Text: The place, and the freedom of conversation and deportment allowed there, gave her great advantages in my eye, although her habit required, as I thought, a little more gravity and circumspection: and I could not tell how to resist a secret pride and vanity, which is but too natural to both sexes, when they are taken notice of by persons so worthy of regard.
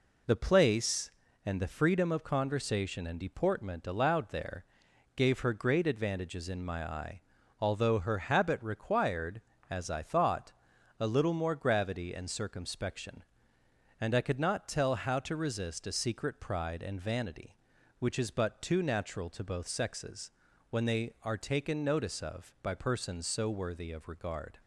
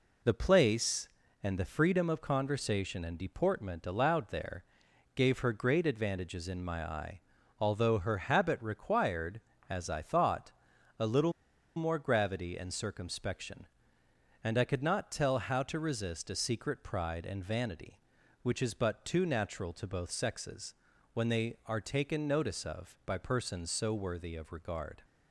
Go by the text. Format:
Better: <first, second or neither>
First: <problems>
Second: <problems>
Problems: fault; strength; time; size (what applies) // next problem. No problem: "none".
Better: first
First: none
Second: pauses between "little" and "more"; at 11.3 s; 0.44 s long